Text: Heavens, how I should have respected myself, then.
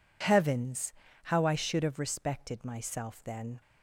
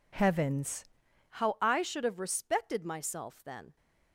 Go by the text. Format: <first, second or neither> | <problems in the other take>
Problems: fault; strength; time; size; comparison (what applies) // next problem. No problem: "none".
first | changes voice at "how"; from 1.3 s on; 2.4 s long